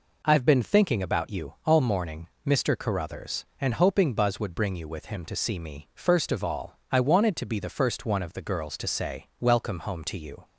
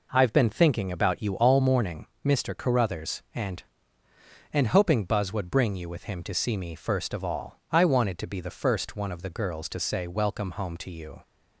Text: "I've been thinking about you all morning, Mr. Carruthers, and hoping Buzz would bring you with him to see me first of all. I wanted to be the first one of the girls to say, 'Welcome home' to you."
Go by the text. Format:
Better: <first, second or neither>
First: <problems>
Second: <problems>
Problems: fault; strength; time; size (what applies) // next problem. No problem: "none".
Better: first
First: none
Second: says "and" twice; at 4.5 s